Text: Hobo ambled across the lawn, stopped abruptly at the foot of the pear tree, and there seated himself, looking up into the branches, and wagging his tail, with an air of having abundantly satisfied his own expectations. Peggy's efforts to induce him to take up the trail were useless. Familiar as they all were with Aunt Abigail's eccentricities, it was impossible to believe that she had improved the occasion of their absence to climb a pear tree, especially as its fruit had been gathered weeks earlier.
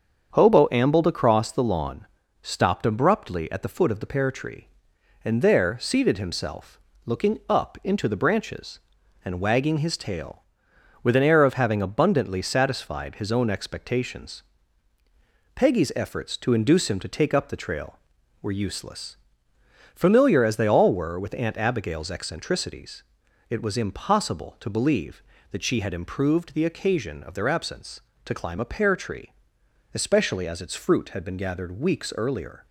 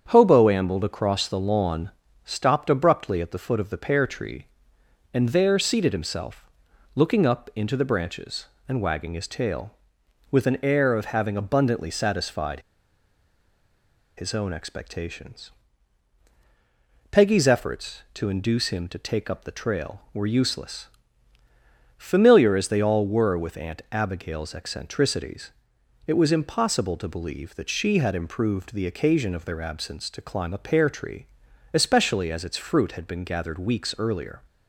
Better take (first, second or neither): first